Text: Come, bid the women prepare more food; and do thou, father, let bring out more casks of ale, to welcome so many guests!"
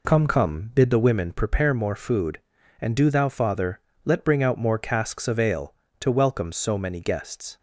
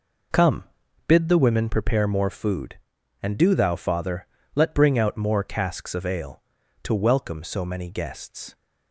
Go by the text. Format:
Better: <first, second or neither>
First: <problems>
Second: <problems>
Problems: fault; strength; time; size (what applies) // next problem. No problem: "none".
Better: second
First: says "Come" twice; at 0.2 s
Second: none